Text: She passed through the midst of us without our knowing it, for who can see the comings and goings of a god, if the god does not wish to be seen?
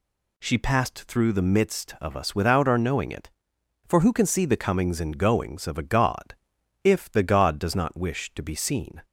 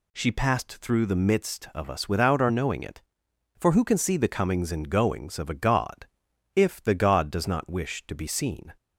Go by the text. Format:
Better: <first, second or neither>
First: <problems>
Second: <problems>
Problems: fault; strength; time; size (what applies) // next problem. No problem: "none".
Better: neither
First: none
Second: none